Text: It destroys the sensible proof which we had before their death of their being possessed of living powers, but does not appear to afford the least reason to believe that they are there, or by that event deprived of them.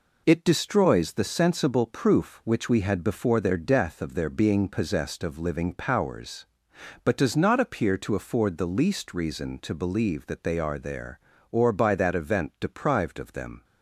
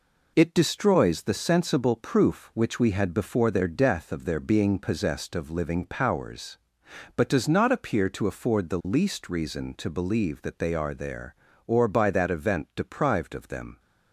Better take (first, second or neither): neither